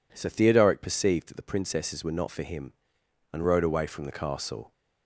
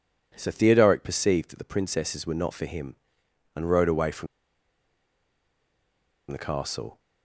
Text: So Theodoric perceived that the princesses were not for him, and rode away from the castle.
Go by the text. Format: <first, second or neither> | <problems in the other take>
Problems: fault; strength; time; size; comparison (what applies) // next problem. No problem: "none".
first | pauses between "from" and "the"; strong; at 4.2 s; 2.0 s long